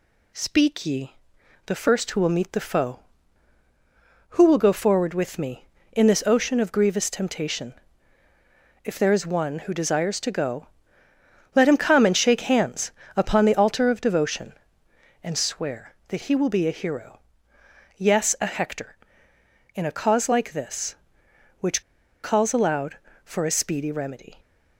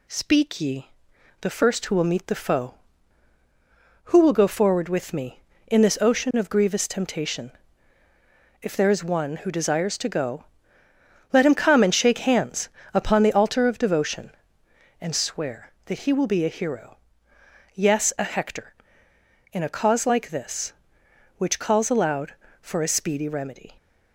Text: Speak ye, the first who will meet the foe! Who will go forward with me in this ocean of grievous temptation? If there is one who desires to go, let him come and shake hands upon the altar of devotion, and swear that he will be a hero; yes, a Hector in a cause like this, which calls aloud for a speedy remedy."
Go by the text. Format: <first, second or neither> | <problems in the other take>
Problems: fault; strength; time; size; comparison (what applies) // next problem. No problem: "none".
second | pauses between "hands" and "upon"; slight; at 12.9 s; 0.24 s long; slight in the second // pauses between "which" and "calls"; at 21.8 s; 0.40 s long